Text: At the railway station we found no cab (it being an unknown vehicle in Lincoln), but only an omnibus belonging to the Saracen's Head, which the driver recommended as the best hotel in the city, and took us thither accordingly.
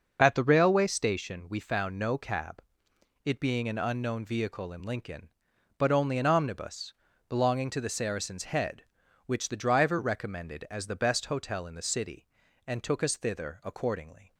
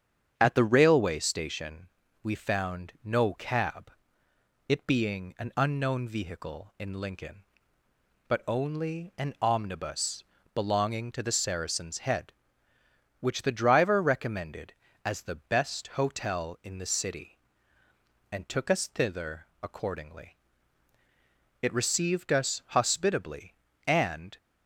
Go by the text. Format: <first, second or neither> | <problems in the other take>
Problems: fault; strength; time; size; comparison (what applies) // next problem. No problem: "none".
first | starts louder than the rest; strong; until 1.3 s; 8 dB // pauses between "station" and "we"; slight; at 1.8 s; 0.34 s long // pauses between "omnibus" and "belonging"; slight; at 10.2 s; 0.28 s long; also in the first // pauses between "thither" and "accordingly"; slight; at 19.4 s; 0.16 s long // goes on to say "It received us hospitably and"; strong; from 21.6 s on; 2.7 s long